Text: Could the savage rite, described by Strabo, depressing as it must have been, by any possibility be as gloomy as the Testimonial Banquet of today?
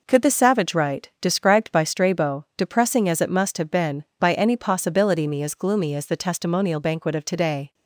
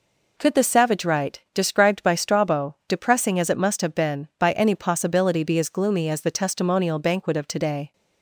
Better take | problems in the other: second | says "me" for "be"; at 5.2 s

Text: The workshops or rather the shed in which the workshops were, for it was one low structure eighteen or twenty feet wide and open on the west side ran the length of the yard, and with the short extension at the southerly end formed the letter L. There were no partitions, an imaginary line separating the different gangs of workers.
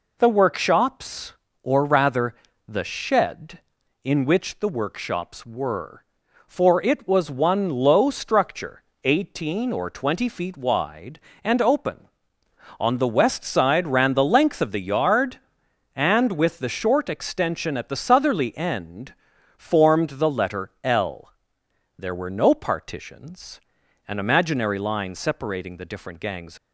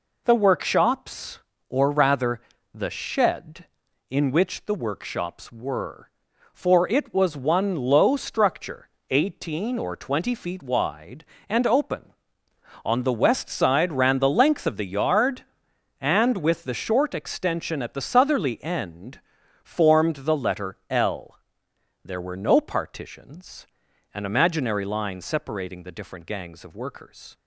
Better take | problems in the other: second | pauses between "rather" and "the"; slight; at 2.3 s; 0.34 s long; slight in the second // pauses between "structure" and "eighteen"; slight; at 8.8 s; 0.22 s long; slight in the second // pauses between "end" and "formed"; at 19.1 s; 0.44 s long; also in the second // stops before "of workers"; at 26.5 s

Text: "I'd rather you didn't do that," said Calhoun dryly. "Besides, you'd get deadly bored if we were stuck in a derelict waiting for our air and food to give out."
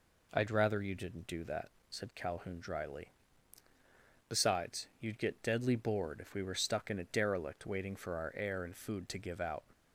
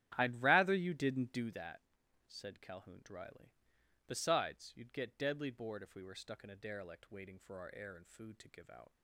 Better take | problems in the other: first | starts louder than the rest; strong; until 1.7 s; 11.5 dB

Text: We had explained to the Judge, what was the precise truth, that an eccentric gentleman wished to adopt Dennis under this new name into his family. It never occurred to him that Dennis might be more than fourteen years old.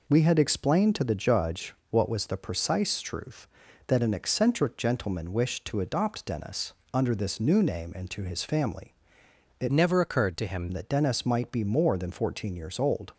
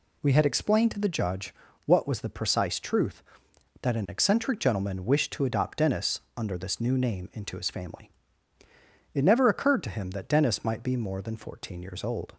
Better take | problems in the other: second | pauses between "Dennis" and "under"; slight; at 6.7 s; 0.20 s long; slight in the second // changes voice from "never" to "him"; from 9.7 to 10.6 s; 0.9 s long

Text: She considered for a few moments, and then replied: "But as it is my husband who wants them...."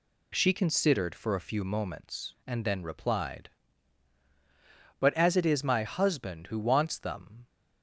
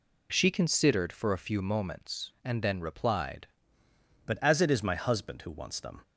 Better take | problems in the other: first | changes voice at "But"; from 4.2 s on; 1.8 s long

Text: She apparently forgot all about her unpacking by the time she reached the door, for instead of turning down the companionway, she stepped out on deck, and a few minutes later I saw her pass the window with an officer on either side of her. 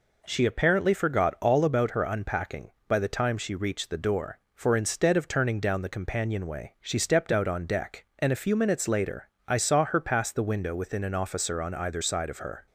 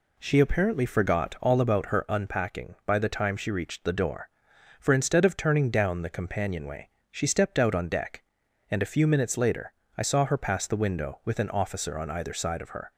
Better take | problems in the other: second | pauses between "later" and "I"; slight; at 9.2 s; 0.20 s long; slight in the second // says "within" for "with"; at 10.7 s

